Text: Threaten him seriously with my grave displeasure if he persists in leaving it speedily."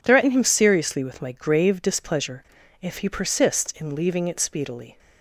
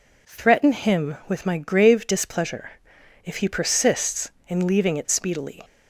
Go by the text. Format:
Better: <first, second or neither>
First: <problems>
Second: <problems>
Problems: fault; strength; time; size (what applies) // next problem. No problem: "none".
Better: first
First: pauses between "displeasure" and "if"; at 2.4 s; 0.37 s long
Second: skips "seriously"; at 1.2 s // pauses between "displeasure" and "if"; noticeable; at 2.7 s; 0.54 s long